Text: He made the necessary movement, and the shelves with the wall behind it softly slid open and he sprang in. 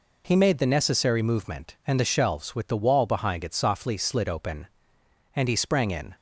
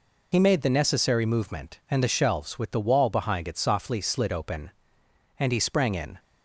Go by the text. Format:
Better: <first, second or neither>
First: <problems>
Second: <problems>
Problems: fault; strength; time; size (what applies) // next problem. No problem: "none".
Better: first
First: none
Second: loses the start of "He"; at 0.3 s; 40 ms